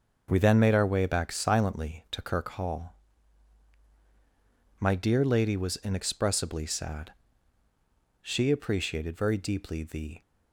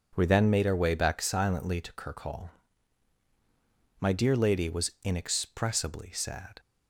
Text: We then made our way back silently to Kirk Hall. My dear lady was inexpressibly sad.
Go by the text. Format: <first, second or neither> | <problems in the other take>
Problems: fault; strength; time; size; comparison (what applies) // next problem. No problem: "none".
second | starts louder than the rest; until 1.3 s; 6 dB // goes on to say "She appreciated very deeply the"; strong; from 8.2 s on; 2.0 s long